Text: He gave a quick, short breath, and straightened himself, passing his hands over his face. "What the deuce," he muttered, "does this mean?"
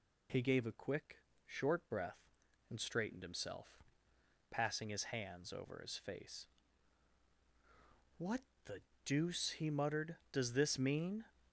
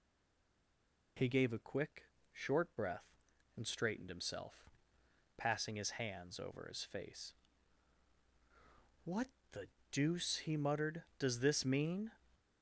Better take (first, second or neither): first